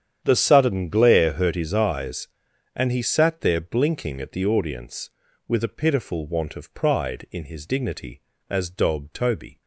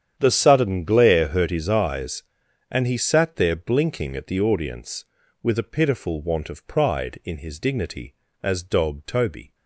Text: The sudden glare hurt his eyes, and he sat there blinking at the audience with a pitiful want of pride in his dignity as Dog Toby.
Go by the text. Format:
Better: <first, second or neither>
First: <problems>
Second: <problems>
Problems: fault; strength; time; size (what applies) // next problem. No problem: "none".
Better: neither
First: starts louder than the rest; strong; until 1.2 s; 9 dB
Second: starts louder than the rest; strong; until 1.1 s; 9 dB